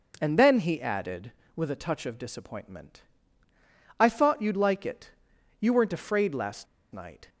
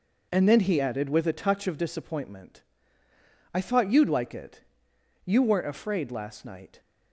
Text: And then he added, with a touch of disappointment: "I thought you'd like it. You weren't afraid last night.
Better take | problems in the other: second | pauses between "last" and "night"; slight; at 6.6 s; 0.27 s long

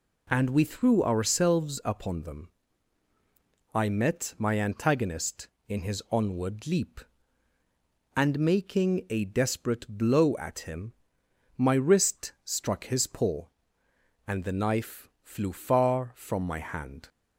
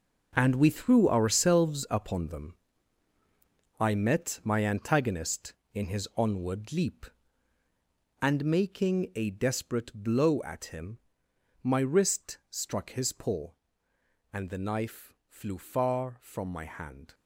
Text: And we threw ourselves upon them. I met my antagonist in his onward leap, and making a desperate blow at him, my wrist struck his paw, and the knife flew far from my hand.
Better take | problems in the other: first | gets quieter; strong; throughout; 11 dB

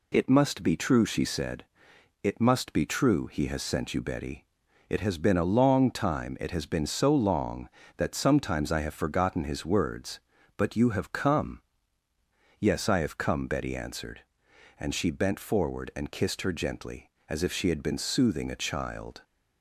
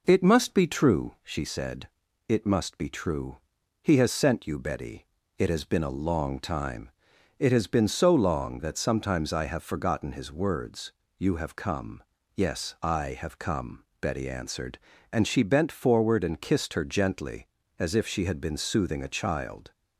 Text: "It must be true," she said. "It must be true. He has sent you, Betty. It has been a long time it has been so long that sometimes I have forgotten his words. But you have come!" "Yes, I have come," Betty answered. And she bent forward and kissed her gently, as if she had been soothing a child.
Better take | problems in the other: first | pauses between "time" and "it"; noticeable; at 6.8 s; 0.48 s long // skips "But"; at 11.0 s

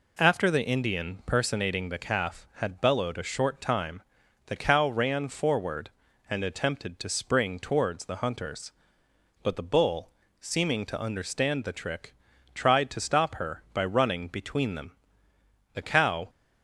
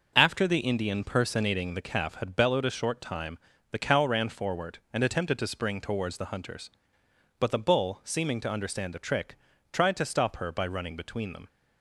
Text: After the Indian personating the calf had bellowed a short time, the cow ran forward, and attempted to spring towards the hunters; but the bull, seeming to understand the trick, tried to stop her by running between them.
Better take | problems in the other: second | goes on to say "The cow"; from 15.7 s on; 0.56 s long

